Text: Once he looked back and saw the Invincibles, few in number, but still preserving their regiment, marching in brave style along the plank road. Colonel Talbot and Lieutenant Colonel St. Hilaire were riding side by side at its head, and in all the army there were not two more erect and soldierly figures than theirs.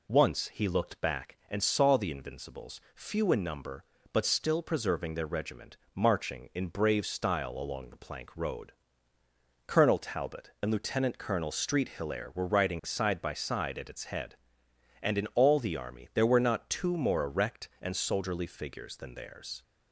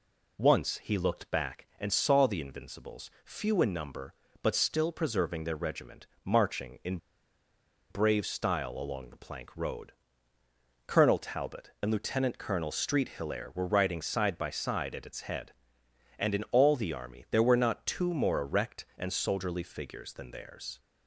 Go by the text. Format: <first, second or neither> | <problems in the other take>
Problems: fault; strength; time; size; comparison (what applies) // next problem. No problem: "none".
first | pauses between "in" and "brave"; noticeable; at 6.9 s; 0.92 s long